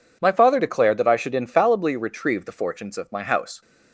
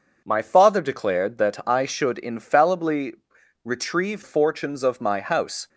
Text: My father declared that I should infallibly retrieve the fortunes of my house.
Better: first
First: none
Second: pauses between "infallibly" and "retrieve"; noticeable; at 3.1 s; 0.50 s long // skips "the"; at 4.2 s

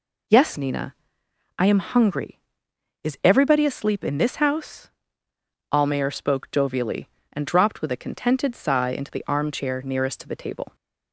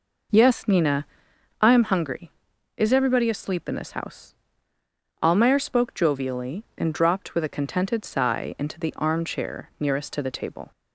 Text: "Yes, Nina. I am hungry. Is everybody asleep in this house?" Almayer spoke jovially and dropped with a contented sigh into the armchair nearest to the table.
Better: first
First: none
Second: starts louder than the rest; noticeable; until 1.4 s; 5 dB

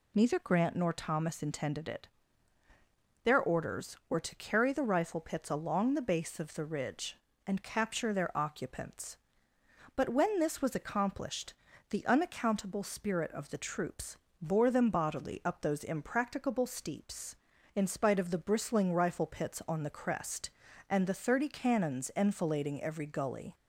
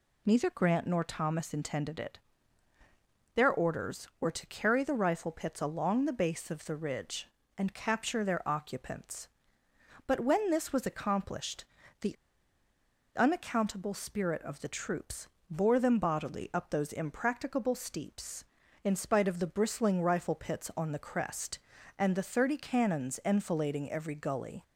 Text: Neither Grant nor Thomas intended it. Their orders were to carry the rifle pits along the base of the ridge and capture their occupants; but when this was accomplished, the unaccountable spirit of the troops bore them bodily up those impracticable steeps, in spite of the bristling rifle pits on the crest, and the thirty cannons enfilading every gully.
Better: first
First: pauses between "troops" and "bore"; slight; at 14.1 s; 0.26 s long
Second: pauses between "the" and "unaccountable"; at 12.1 s; 1.0 s long // pauses between "troops" and "bore"; slight; at 15.2 s; 0.24 s long

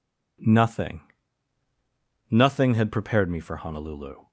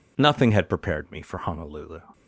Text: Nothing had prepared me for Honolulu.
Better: second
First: says "Nothing" twice; at 2.3 s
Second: none

